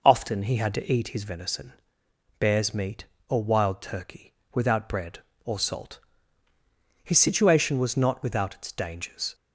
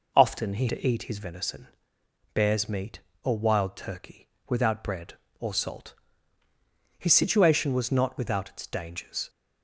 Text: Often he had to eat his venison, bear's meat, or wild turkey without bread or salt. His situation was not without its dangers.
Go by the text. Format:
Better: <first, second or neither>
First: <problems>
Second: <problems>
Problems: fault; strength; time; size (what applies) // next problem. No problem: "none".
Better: first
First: pauses between "turkey" and "without"; slight; at 4.3 s; 0.22 s long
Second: skips "had"; at 0.6 s // pauses between "turkey" and "without"; slight; at 4.2 s; 0.22 s long